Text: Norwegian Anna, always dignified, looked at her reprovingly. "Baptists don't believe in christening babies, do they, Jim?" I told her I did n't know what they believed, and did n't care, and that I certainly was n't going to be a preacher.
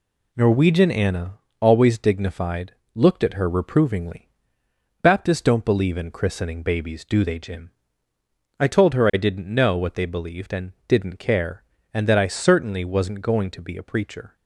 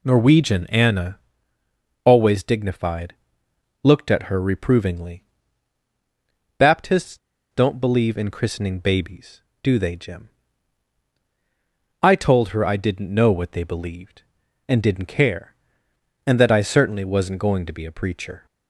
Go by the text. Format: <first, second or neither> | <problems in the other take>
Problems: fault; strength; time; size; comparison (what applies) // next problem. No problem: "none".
first | pauses between "Baptists" and "don't"; slight; at 7.1 s; 0.33 s long